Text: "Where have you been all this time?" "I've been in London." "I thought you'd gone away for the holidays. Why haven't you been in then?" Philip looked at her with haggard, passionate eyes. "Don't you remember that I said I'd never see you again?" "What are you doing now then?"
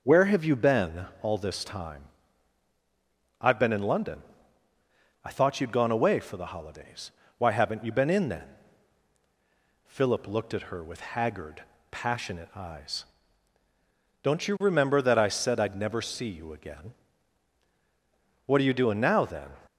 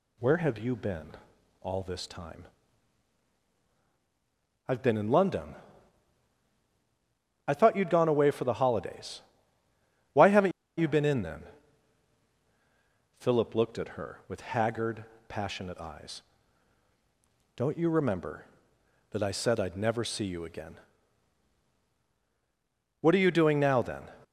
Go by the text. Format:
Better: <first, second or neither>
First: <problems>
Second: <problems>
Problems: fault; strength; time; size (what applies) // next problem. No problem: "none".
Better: first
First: pauses between "been" and "all"; slight; at 1.0 s; 0.16 s long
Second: pauses between "been" and "all"; noticeable; at 1.1 s; 0.48 s long // pauses between "haven't" and "you"; slight; at 10.5 s; 0.28 s long